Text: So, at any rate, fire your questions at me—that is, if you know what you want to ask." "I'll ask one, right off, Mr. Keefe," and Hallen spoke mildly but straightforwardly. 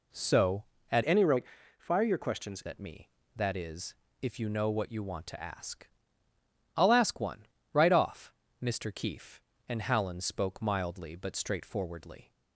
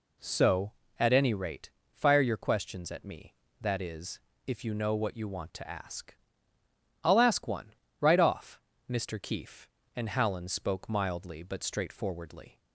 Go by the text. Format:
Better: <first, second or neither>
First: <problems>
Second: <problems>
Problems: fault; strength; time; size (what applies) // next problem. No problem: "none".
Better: second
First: changes voice from "any" to "questions"; from 1.0 to 2.6 s; 1.6 s long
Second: none